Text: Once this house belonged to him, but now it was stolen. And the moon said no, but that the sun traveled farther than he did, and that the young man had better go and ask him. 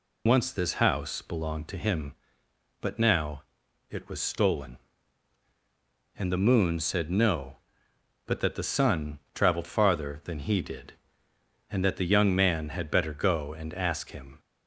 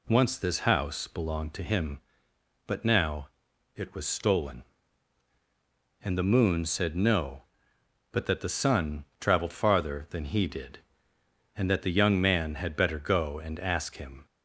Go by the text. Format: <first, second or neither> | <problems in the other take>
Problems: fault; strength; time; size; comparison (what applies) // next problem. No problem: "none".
second | loses the start of "Once"; at 0.2 s; 50 ms // pauses between "now" and "it"; noticeable; at 3.4 s; 0.48 s long; noticeable in the second // pauses between "sun" and "traveled"; slight; at 9.1 s; 0.16 s long; slight in the second